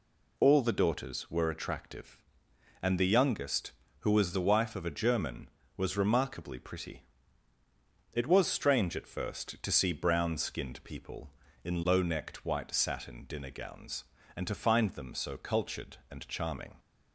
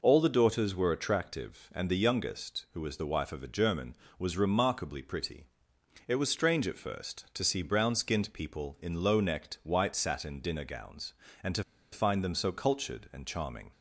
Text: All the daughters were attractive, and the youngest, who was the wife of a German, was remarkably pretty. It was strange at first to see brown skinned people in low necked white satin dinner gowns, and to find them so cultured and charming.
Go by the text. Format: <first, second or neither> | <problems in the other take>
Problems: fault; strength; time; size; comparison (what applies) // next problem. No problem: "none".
first | pauses between "to" and "find"; slight; at 11.6 s; 0.29 s long